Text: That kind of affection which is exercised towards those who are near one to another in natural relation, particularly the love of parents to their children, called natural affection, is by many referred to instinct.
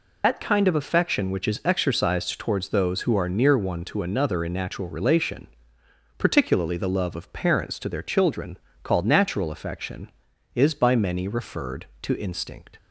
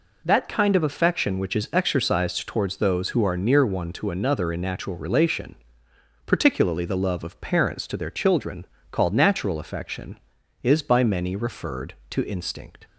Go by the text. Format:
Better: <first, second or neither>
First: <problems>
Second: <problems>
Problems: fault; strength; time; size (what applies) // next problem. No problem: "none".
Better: second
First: loses the start of "That"; at 0.2 s; 80 ms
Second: none